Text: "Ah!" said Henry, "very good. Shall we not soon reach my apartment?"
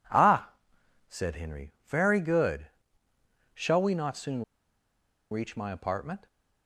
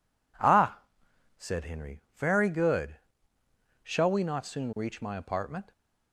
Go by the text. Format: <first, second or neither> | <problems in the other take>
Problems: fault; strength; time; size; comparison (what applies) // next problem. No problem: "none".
second | pauses between "soon" and "reach"; noticeable; at 4.4 s; 0.87 s long